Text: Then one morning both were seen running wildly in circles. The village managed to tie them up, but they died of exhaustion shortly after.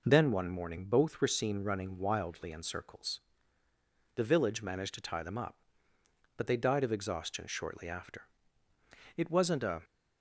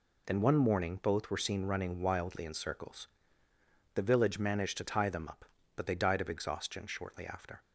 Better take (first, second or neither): second